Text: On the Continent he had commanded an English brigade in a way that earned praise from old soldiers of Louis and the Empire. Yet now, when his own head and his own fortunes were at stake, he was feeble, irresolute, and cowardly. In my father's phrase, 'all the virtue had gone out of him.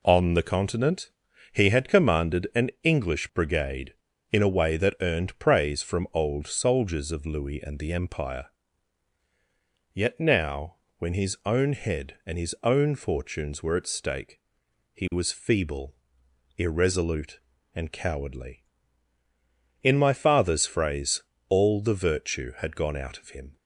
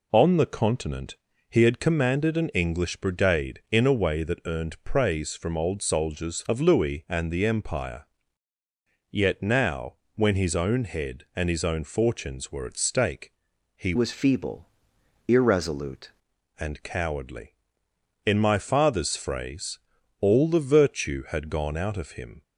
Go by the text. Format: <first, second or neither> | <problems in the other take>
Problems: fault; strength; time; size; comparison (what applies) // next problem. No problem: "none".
first | pauses between "Continent" and "he"; slight; at 1.1 s; 0.34 s long; also in the first // changes voice from "was" to "irresolute"; from 13.9 to 16.1 s; 2.2 s long